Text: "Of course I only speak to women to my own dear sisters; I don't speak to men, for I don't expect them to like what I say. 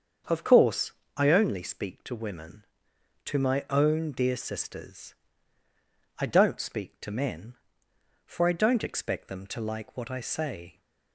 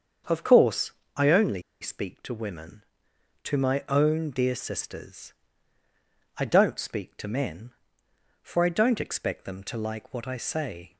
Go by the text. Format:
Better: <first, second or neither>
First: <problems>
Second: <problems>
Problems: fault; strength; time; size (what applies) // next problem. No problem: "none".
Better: first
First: starts louder than the rest; strong; until 1.5 s; 7 dB // pauses between "course" and "I"; slight; at 0.9 s; 0.26 s long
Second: starts louder than the rest; strong; until 1.5 s; 7 dB // pauses between "course" and "I"; slight; at 0.9 s; 0.26 s long // pauses between "only" and "speak"; slight; at 1.6 s; 0.19 s long